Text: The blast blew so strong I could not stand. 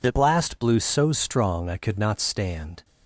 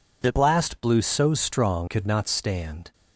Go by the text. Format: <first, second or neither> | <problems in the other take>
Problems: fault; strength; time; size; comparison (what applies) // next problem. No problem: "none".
first | skips "I"; at 1.8 s